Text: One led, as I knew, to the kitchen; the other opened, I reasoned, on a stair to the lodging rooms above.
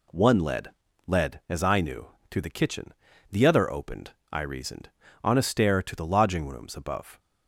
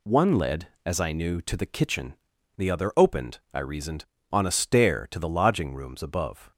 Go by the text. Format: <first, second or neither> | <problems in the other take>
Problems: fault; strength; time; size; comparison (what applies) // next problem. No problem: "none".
second | says "led" twice; at 1.0 s